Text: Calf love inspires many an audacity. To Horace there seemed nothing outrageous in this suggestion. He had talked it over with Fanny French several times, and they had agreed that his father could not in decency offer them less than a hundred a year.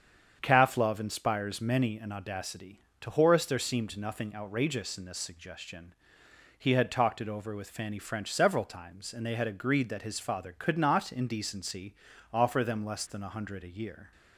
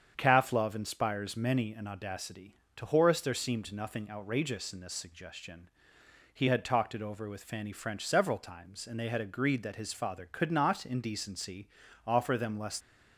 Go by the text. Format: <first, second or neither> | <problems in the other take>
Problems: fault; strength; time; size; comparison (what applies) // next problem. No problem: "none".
first | starts louder than the rest; strong; until 1.1 s; 7.5 dB; strong in the first // pauses between "decency" and "offer"; at 11.6 s; 0.40 s long; also in the first // stops before "than a hundred a year"; at 12.8 s